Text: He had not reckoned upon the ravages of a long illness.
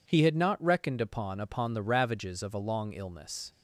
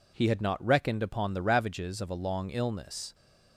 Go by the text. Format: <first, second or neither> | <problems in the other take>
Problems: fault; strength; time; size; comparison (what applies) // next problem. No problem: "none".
second | says "upon" twice; at 1.4 s